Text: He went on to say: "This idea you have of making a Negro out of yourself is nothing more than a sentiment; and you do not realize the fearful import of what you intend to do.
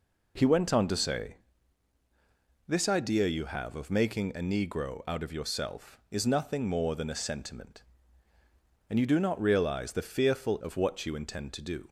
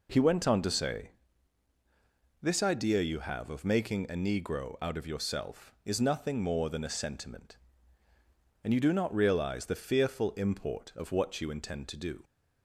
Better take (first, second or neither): second